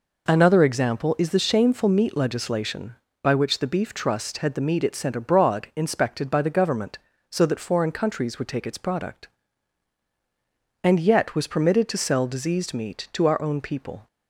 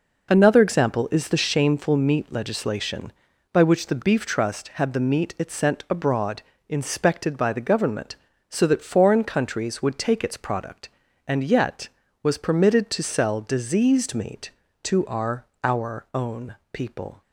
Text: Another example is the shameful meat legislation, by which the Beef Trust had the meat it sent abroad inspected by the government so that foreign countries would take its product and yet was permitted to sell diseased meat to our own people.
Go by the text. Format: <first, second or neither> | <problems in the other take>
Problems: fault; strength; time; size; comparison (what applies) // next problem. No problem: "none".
first | pauses between "abroad" and "inspected"; slight; at 6.4 s; 0.24 s long // says "our" twice; at 15.6 s // pauses between "own" and "people"; slight; at 16.5 s; 0.18 s long